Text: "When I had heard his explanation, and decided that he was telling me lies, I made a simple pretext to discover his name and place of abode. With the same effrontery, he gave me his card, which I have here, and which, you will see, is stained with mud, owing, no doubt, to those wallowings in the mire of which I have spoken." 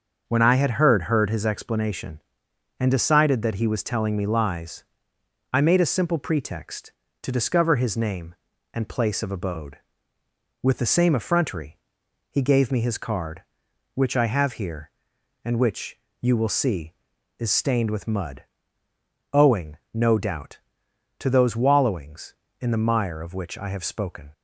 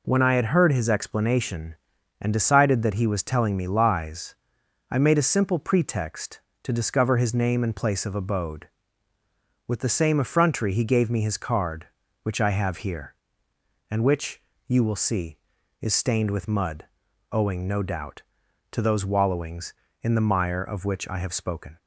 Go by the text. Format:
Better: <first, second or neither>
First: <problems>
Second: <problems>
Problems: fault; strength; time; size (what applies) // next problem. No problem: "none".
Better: second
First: starts louder than the rest; until 1.2 s; 6.5 dB // says "heard" twice; at 1.0 s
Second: none